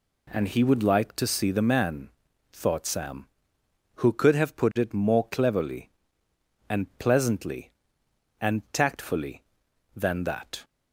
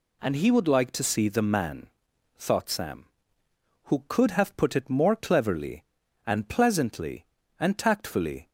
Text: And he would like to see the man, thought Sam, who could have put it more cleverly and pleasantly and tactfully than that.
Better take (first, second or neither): first